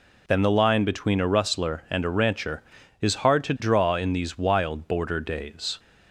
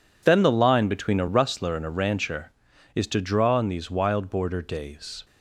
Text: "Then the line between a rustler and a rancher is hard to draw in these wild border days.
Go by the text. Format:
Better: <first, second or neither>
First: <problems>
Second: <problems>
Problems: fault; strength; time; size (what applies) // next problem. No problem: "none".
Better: first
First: none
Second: skips "hard"; at 3.0 s